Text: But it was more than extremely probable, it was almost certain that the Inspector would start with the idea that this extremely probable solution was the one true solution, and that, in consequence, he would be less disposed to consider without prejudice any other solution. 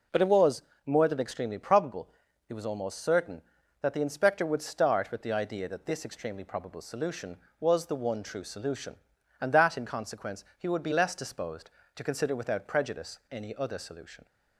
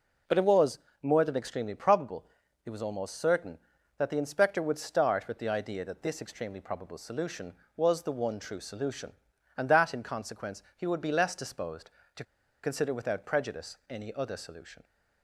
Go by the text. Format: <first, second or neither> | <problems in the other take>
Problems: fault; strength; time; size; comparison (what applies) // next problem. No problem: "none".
first | pauses between "was" and "more"; slight; at 0.7 s; 0.24 s long; slight in the first // pauses between "to" and "consider"; at 12.2 s; 0.39 s long